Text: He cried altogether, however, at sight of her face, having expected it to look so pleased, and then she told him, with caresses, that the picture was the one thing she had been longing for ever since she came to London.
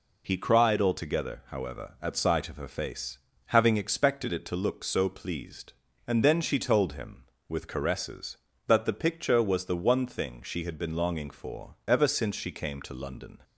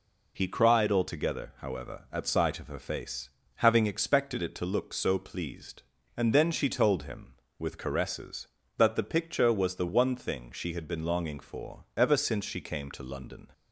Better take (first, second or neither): neither